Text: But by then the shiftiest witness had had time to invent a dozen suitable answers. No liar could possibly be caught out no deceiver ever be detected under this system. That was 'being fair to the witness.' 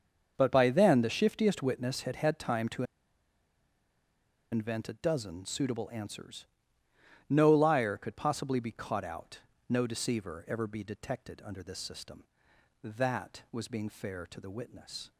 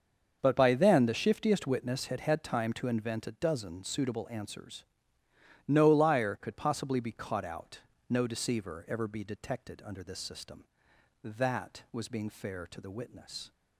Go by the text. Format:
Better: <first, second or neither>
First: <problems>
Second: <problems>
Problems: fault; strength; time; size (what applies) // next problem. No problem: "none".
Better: second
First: starts louder than the rest; until 1.3 s; 6.5 dB // pauses between "to" and "invent"; strong; at 2.8 s; 1.6 s long // pauses between "out" and "no"; slight; at 9.3 s; 0.30 s long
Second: starts louder than the rest; until 1.4 s; 6.5 dB // pauses between "out" and "no"; slight; at 7.7 s; 0.30 s long